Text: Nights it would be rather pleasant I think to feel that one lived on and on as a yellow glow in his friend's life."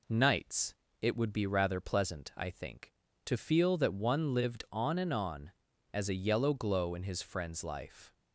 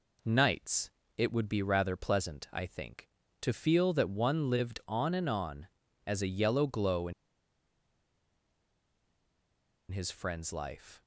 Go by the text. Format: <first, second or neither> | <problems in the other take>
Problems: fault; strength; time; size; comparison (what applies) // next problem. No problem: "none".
first | pauses between "Nights" and "it"; slight; at 0.8 s; 0.26 s long; slight in the first // pauses between "in" and "his"; strong; at 7.1 s; 2.7 s long